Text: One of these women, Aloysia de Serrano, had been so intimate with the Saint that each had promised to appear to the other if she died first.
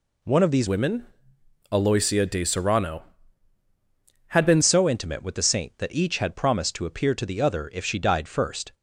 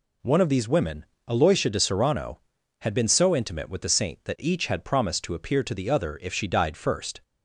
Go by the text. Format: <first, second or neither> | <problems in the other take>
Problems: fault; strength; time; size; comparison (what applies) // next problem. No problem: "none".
second | changes voice from "women" to "been"; from 0.6 to 4.6 s; 4.0 s long